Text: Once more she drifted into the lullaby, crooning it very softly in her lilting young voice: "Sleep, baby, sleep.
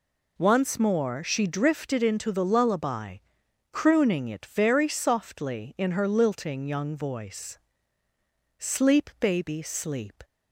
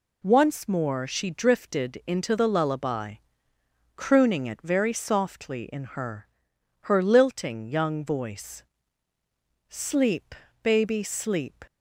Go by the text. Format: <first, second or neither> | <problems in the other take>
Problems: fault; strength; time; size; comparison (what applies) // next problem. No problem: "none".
first | says "her" twice; at 6.8 s